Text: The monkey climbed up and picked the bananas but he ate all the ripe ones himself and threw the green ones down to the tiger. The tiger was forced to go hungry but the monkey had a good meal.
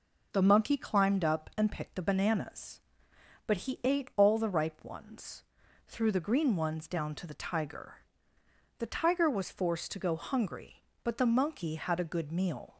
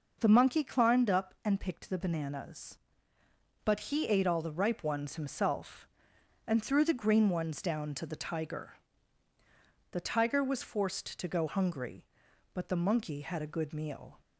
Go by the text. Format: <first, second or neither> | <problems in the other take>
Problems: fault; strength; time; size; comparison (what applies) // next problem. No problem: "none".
second | skips "himself and"; at 5.6 s